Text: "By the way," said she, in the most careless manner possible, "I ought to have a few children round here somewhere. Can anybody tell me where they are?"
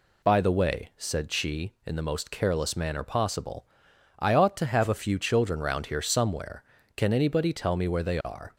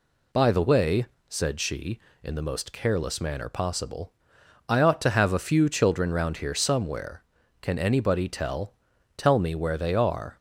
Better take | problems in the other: first | says "tell" twice; at 9.1 s

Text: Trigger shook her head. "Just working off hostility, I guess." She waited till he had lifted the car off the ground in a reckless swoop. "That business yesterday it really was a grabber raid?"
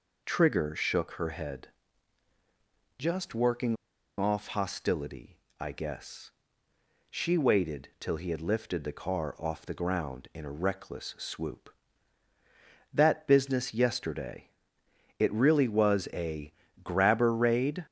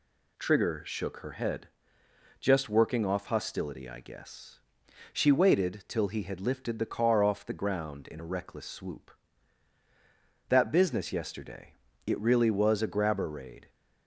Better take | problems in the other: second | pauses between "working" and "off"; at 3.7 s; 0.42 s long // pauses between "yesterday" and "it"; noticeable; at 14.4 s; 0.70 s long; slight in the second // pauses between "a" and "grabber"; slight; at 16.5 s; 0.28 s long

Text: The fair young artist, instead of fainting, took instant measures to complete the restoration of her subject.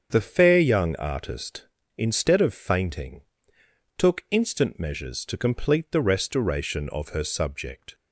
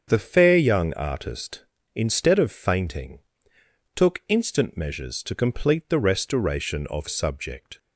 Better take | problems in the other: first | starts louder than the rest; strong; until 1.0 s; 7 dB; strong in the first // skips "her"; at 7.0 s

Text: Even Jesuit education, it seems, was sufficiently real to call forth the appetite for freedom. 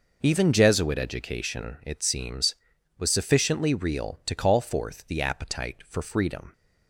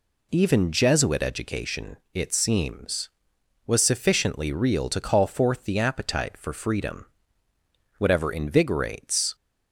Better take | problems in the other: first | goes on to say "Whatever invigorates"; from 7.9 s on; 1.3 s long

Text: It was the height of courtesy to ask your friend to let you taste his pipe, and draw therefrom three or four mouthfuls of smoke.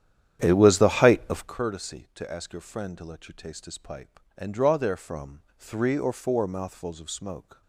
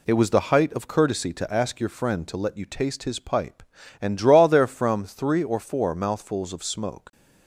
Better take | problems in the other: second | starts louder than the rest; strong; until 1.5 s; 10 dB // pauses between "therefrom" and "three"; slight; at 5.4 s; 0.16 s long

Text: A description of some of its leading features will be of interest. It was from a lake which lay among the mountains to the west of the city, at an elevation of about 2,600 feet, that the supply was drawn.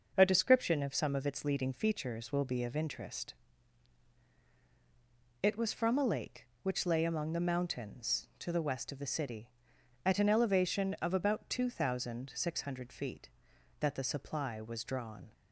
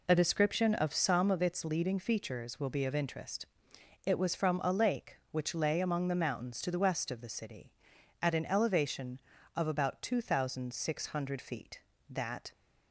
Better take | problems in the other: first | stops before "the supply was drawn"; at 12.5 s

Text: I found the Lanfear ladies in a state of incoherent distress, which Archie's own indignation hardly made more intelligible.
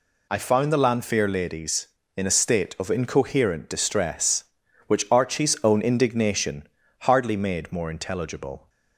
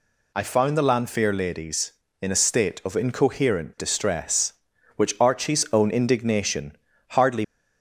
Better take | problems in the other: first | pauses between "indignation" and "hardly"; slight; at 6.7 s; 0.36 s long; slight in the first // stops before "made more intelligible"; at 7.4 s

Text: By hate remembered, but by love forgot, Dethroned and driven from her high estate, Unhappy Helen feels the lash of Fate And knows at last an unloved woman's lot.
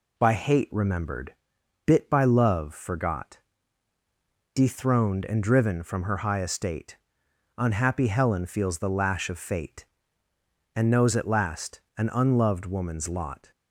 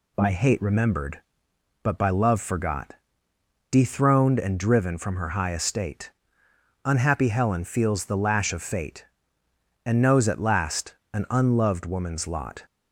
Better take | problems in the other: second | says "bit" for "but"; at 1.8 s // pauses between "last" and "an"; slight; at 11.8 s; 0.18 s long; slight in the second

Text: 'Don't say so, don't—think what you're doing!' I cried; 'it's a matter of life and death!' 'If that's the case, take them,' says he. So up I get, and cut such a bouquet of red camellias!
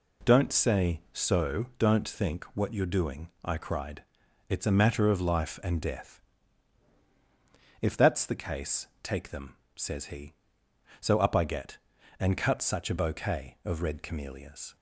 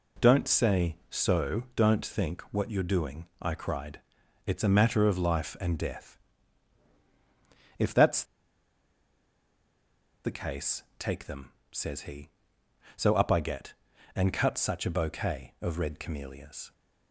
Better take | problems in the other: first | pauses between "that's" and "the"; strong; at 8.2 s; 2.0 s long

